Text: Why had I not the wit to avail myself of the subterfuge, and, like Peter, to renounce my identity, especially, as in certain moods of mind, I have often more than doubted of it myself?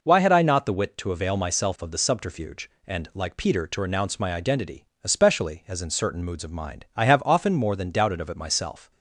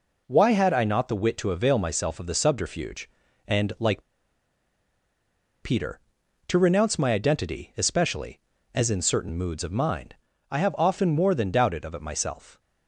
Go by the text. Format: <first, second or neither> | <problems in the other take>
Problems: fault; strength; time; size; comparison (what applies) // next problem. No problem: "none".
first | pauses between "like" and "Peter"; strong; at 4.0 s; 1.6 s long